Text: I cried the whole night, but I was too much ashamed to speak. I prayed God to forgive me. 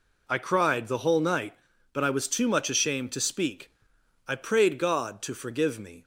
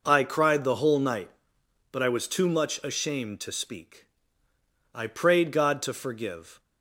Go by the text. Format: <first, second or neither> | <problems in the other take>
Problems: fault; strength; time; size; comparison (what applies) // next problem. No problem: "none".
first | stops before "me"; at 6.5 s